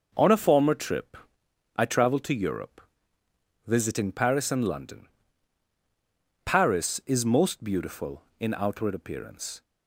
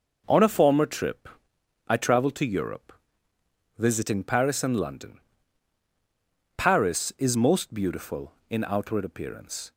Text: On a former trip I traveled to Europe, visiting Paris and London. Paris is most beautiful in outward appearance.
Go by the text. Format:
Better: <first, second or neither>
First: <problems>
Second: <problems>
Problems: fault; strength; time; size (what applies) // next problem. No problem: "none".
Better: neither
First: pauses between "trip" and "I"; noticeable; at 1.1 s; 0.58 s long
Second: pauses between "trip" and "I"; noticeable; at 1.2 s; 0.58 s long